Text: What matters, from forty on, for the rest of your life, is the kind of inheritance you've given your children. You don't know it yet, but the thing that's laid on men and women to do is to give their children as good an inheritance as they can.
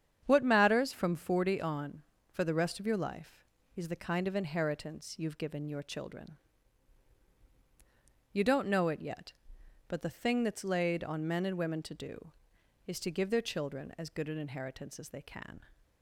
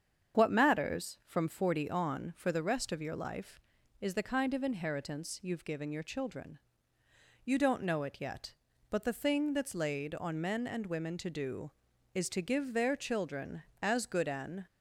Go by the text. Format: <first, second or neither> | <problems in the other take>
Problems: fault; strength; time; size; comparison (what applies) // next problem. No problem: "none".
first | starts louder than the rest; strong; until 1.4 s; 7.5 dB; strong in the first // stops before "inheritance as they can"; at 14.6 s